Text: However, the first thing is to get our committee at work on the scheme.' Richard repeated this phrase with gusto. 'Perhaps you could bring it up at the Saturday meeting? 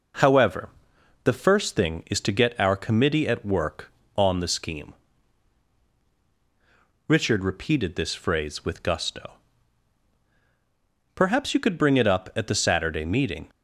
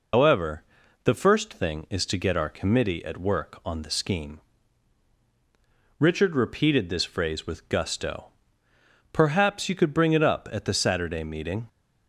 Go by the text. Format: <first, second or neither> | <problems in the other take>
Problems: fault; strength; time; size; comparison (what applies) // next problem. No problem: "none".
first | loses the start of "However"; at 0.1 s; 115 ms